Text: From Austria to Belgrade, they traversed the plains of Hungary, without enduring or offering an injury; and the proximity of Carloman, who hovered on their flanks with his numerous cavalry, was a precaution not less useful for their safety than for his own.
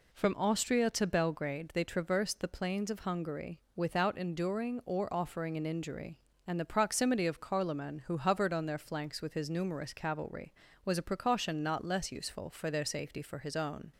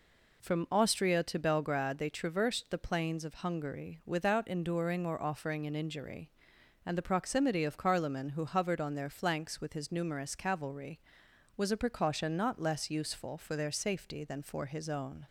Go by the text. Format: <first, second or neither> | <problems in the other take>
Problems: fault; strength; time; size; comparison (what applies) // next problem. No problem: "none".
second | skips "than"; at 13.2 s